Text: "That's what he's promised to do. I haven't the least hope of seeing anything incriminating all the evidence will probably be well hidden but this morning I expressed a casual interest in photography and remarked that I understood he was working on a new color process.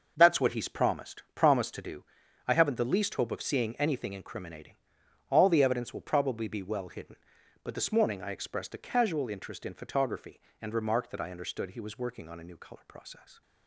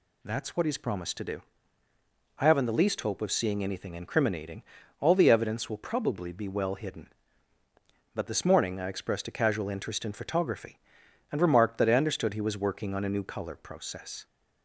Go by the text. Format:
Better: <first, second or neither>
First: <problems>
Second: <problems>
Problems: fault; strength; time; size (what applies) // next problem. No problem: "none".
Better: second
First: says "promised" twice; at 1.3 s // pauses between "incriminating" and "all"; noticeable; at 4.7 s; 0.52 s long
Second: pauses between "incriminating" and "all"; at 4.6 s; 0.38 s long